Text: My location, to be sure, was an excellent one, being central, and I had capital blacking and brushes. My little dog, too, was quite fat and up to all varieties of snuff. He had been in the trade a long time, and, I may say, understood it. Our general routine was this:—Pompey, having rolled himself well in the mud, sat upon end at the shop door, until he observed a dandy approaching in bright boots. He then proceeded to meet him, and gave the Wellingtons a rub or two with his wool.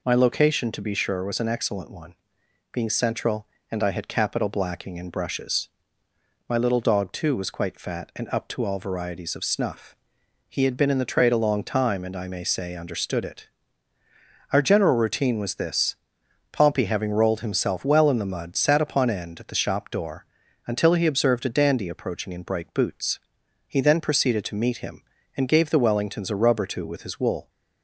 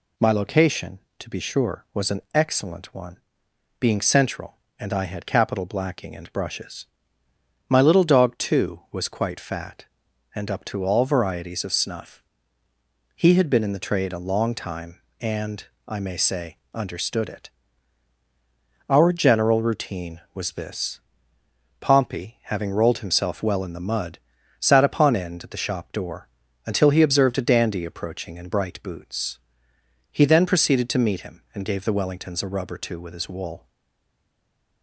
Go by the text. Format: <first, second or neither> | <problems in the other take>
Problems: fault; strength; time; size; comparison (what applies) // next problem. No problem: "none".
first | stays silent after the last word; noticeable; from 33.6 s on; 1.2 s long